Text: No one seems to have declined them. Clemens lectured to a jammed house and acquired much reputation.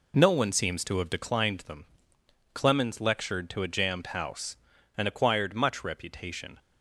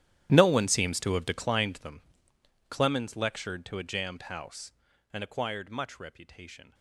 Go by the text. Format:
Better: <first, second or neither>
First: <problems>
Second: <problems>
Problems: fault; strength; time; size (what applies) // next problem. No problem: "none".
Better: first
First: none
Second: gets quieter; strong; throughout; 18.5 dB